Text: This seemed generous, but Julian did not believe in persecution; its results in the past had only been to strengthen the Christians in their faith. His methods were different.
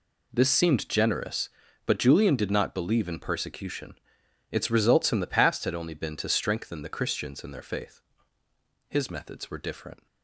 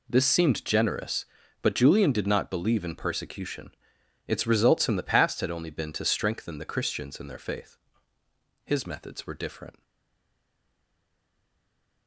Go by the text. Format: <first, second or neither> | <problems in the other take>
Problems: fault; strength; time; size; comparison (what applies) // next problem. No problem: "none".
first | stays silent after the last word; from 9.8 s on; 2.2 s long